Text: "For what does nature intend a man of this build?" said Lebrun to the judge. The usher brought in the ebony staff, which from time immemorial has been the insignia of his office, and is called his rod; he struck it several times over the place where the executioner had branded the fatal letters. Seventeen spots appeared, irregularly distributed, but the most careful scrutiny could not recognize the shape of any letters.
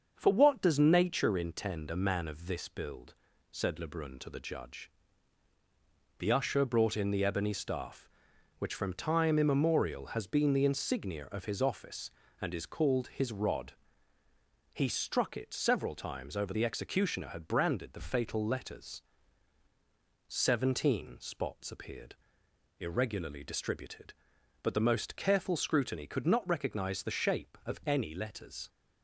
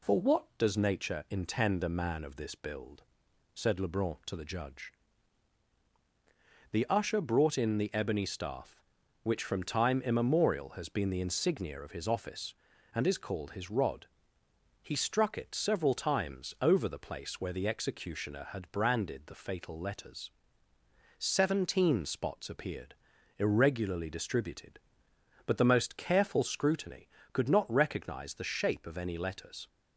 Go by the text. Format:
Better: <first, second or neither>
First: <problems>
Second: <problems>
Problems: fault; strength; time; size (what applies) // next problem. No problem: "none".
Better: second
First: starts louder than the rest; until 1.1 s; 6.5 dB // skips "the place where"; at 16.5 s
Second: none